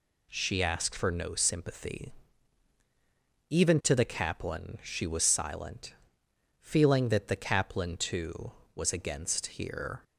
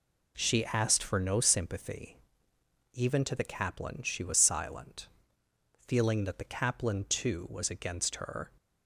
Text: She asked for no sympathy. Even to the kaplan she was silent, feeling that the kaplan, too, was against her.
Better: second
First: says "here" for "her"; at 9.4 s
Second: none

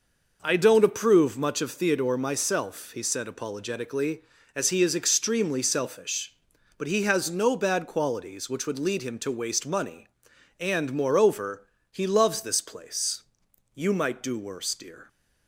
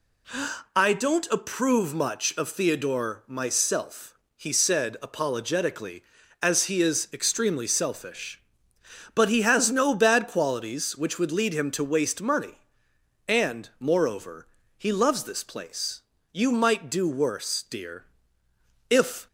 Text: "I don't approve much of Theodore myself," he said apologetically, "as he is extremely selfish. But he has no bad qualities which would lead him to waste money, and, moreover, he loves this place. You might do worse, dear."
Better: first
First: none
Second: goes on to say "If"; slight; from 18.8 s on; 0.38 s long

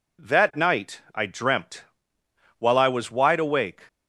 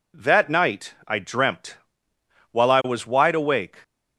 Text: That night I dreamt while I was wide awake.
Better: neither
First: pauses between "night" and "I"; slight; at 1.0 s; 0.16 s long // pauses between "dreamt" and "while"; noticeable; at 1.8 s; 0.78 s long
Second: pauses between "night" and "I"; slight; at 0.9 s; 0.16 s long // pauses between "dreamt" and "while"; noticeable; at 1.7 s; 0.78 s long

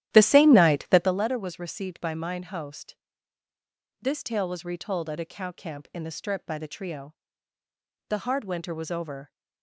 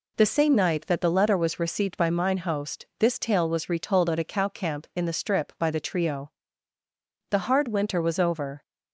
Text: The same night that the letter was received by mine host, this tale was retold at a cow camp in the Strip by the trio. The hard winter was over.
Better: second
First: starts louder than the rest; strong; until 1.2 s; 12.5 dB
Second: none

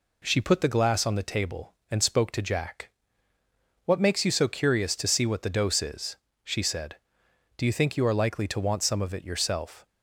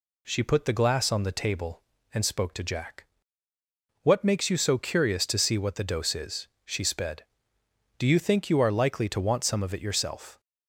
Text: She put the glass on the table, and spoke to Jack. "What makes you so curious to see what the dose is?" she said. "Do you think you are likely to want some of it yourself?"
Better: first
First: none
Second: says "sped" for "said"; at 6.8 s

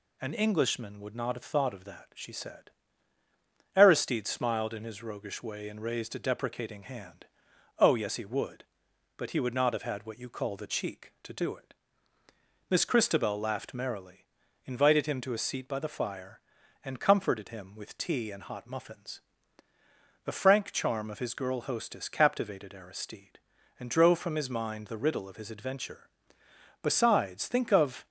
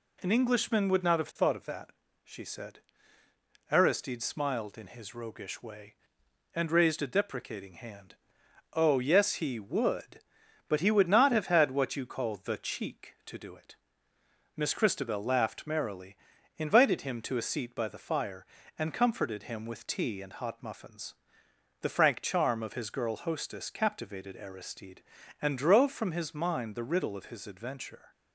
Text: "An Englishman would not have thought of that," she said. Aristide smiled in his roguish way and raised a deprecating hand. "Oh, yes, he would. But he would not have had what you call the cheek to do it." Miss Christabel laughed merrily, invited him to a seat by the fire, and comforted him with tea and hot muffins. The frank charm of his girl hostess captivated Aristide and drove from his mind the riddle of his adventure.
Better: second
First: goes on to say "Besides think of"; noticeable; from 26.8 s on; 1.2 s long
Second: none

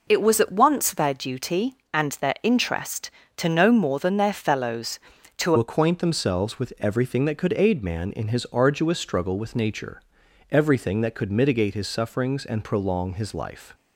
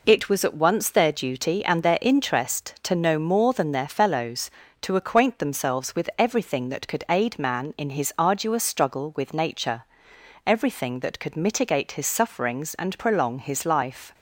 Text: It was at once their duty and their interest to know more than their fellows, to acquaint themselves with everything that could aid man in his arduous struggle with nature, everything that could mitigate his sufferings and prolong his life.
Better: second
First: changes voice at "acquaint"; from 5.5 s on; 8.2 s long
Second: none

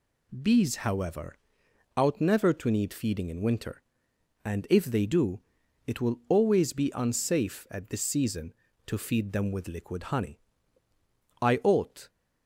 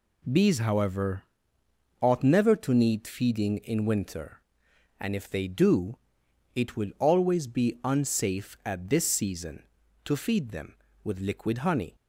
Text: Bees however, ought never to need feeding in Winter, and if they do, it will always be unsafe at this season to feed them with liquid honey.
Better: second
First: goes on to say "I ought"; noticeable; from 11.4 s on; 0.68 s long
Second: none

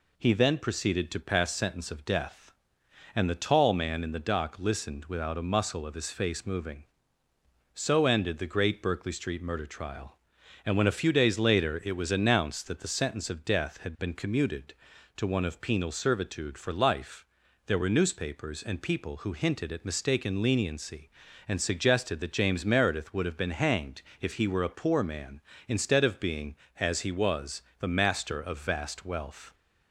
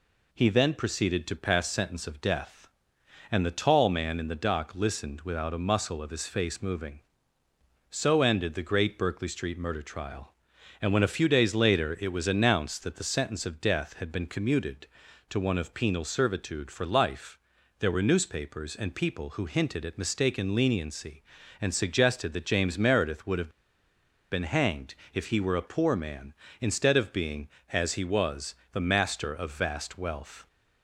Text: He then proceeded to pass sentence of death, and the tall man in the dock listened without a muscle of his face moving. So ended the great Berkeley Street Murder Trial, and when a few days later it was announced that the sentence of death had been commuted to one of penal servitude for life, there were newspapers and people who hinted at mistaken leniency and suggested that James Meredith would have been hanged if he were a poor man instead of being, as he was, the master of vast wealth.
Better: first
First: pauses between "hanged" and "if"; slight; at 24.0 s; 0.18 s long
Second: pauses between "have" and "been"; noticeable; at 23.4 s; 0.82 s long // pauses between "hanged" and "if"; slight; at 24.9 s; 0.18 s long

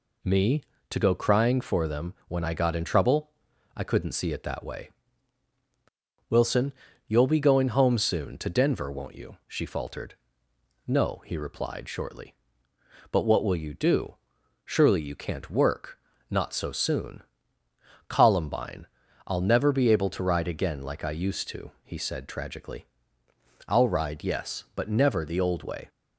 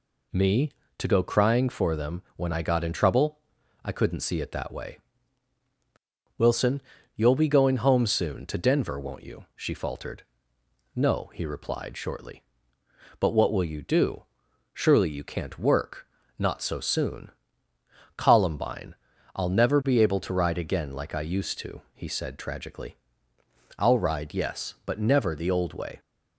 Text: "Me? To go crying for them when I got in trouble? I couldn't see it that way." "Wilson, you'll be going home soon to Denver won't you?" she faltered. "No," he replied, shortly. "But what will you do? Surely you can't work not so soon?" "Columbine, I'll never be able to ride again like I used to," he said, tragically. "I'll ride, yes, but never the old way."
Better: neither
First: pauses between "work" and "not"; slight; at 15.9 s; 0.32 s long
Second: pauses between "work" and "not"; slight; at 16.0 s; 0.32 s long

